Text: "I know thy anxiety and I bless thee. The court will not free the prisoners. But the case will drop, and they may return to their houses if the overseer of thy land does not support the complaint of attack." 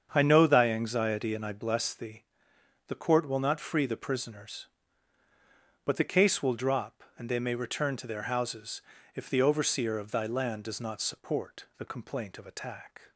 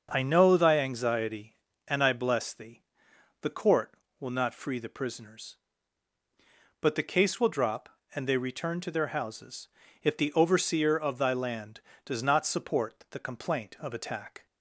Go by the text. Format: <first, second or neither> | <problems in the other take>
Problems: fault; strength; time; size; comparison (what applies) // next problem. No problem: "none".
first | starts louder than the rest; until 1.1 s; 6 dB; strong in the first // skips "may"; at 8.3 s // pauses between "houses" and "if"; slight; at 9.6 s; 0.34 s long; slight in the first